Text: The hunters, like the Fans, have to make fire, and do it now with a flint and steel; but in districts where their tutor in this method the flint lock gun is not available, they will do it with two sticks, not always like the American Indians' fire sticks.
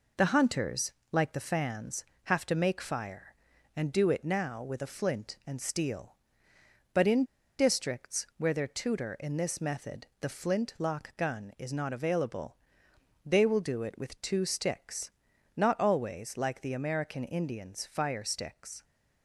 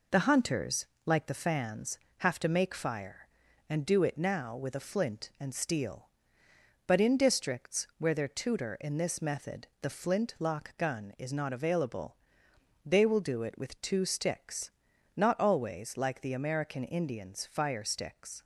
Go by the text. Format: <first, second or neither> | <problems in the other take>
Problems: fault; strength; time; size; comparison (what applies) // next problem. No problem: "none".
second | pauses between "in" and "districts"; slight; at 7.2 s; 0.33 s long // pauses between "method" and "the"; slight; at 10.0 s; 0.16 s long; slight in the second